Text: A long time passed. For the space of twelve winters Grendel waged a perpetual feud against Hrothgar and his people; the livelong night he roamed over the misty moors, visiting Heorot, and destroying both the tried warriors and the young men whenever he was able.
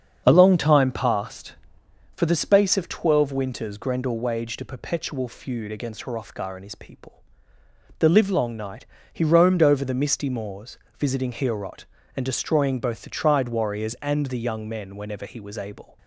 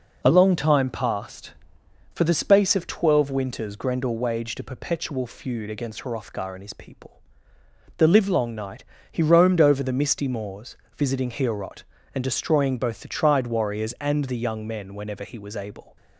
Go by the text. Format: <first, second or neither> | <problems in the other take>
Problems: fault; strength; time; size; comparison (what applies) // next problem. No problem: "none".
second | starts louder than the rest; strong; until 1.5 s; 7 dB // pauses between "night" and "he"; slight; at 8.8 s; 0.26 s long; slight in the second